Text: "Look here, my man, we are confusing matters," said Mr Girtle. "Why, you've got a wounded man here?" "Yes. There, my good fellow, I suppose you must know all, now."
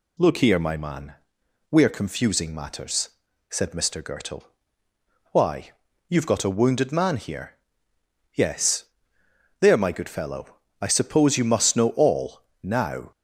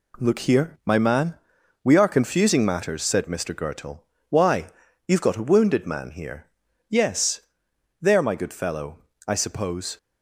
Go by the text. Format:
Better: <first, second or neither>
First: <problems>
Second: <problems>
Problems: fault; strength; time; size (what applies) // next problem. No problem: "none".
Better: first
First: none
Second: stops before "you must know all now"; at 9.9 s